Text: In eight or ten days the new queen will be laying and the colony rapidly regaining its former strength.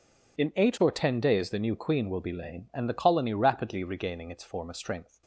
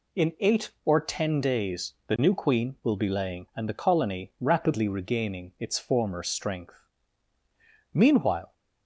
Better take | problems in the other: first | pauses between "days" and "the"; slight; at 1.9 s; 0.16 s long // goes on to say "Meanwhile"; from 7.9 s on; 0.58 s long

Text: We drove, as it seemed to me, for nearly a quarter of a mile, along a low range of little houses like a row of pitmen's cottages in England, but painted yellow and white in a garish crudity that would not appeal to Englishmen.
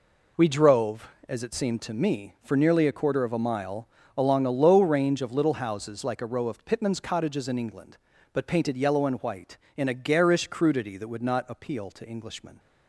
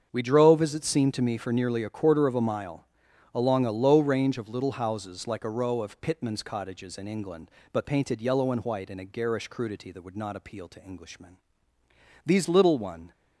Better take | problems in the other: first | starts louder than the rest; strong; until 1.1 s; 7 dB // goes on to say "These little one"; noticeable; from 12.2 s on; 0.86 s long

